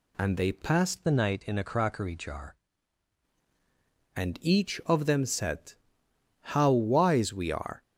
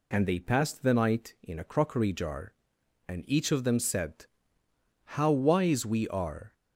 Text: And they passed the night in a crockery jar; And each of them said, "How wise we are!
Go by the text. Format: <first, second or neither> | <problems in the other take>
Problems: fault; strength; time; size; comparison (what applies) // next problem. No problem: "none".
second | changes voice from "the" to "jar"; from 1.0 to 2.5 s; 1.5 s long